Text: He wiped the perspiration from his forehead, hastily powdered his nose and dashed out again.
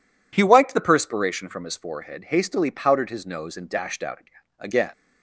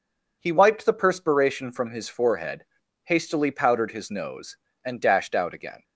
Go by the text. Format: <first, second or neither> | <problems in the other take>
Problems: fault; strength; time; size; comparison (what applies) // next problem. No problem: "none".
second | says "again" twice; at 4.5 s